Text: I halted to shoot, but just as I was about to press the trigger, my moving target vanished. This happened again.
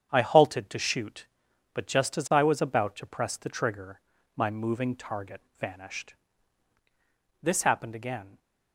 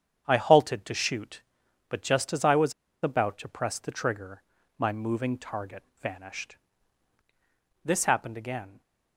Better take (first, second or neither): first